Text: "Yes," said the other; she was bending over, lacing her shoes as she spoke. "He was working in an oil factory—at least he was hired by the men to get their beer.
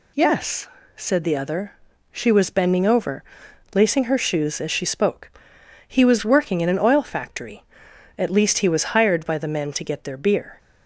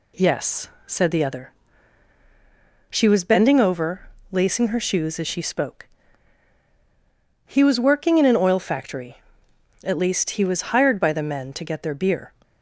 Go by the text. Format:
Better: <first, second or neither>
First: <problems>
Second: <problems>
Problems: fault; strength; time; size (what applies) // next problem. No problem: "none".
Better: neither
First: none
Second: none